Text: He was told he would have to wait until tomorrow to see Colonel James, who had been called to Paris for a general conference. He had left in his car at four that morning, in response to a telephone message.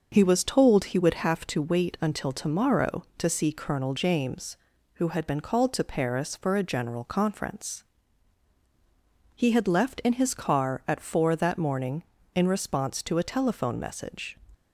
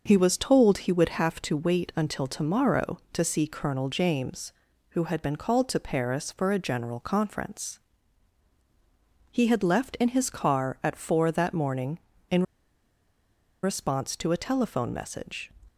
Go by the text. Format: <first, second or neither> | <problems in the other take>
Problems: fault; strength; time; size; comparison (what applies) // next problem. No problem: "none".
first | starts louder than the rest; noticeable; until 1.0 s; 6 dB; noticeable in the first // pauses between "in" and "response"; at 12.4 s; 1.1 s long